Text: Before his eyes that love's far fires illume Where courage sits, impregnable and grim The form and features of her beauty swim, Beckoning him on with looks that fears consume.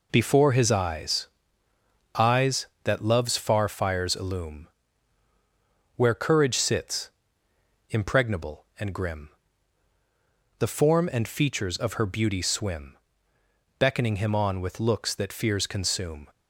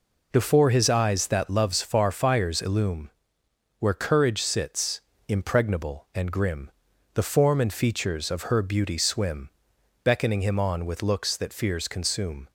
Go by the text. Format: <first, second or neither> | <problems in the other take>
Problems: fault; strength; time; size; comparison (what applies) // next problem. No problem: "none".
second | says "eyes" twice; at 2.1 s // pauses between "illume" and "Where"; strong; at 4.6 s; 1.3 s long; noticeable in the second // pauses between "grim" and "The"; strong; at 9.2 s; 1.2 s long; also in the second